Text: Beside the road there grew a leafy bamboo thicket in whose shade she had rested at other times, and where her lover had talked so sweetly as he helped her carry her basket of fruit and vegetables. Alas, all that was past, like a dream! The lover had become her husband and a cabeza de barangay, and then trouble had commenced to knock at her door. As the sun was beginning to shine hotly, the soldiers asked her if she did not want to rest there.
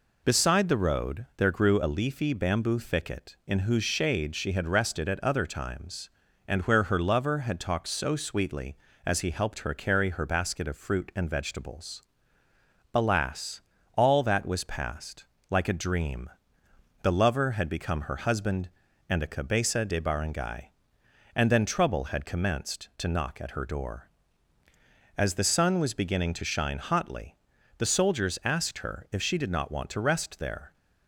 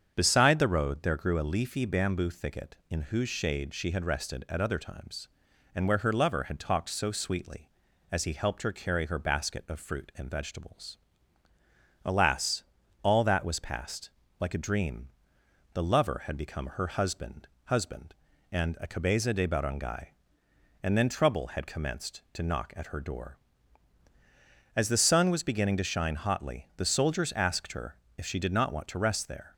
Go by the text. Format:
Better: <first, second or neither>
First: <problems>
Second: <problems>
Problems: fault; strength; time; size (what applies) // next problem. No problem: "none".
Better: first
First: none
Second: starts louder than the rest; strong; until 1.1 s; 7.5 dB // says "husband" twice; at 17.6 s // pauses between "her" and "if"; slight; at 27.9 s; 0.24 s long